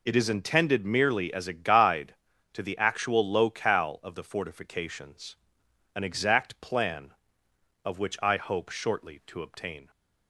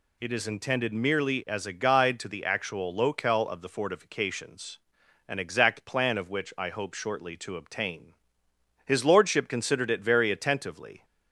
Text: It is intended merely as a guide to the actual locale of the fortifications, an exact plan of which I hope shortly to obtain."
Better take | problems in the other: first | goes on to say "His lordship considered it very attentively"; strong; from 8.8 s on; 2.2 s long

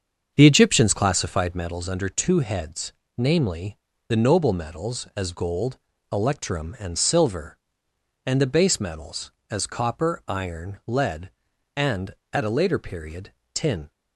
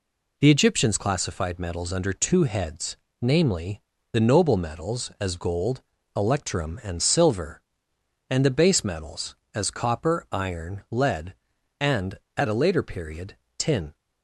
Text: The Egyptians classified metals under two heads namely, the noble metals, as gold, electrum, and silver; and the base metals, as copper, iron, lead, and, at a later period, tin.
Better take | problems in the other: second | starts louder than the rest; until 1.7 s; 7 dB // pauses between "heads" and "namely"; slight; at 2.9 s; 0.22 s long; slight in the second

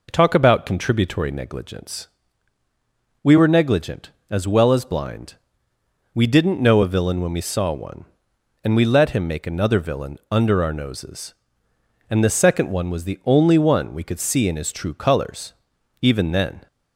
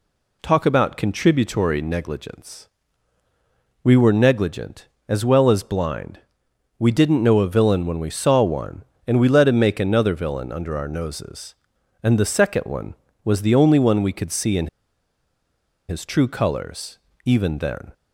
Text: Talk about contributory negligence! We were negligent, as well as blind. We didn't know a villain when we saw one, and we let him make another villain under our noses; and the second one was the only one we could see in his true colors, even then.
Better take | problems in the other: first | pauses between "in" and "his"; at 14.6 s; 1.2 s long

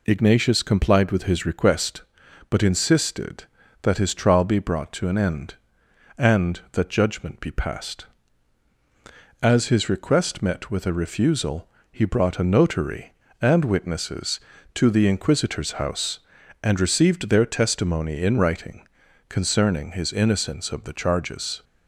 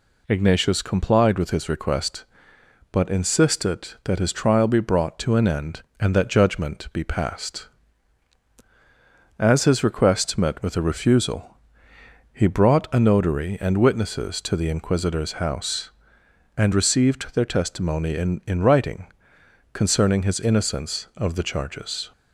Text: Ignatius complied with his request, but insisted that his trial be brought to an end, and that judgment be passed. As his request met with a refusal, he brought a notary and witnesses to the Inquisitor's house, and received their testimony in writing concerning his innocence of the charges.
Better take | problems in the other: first | says "in" twice; at 18.4 s // pauses between "writing" and "concerning"; noticeable; at 19.0 s; 0.66 s long; also in the first

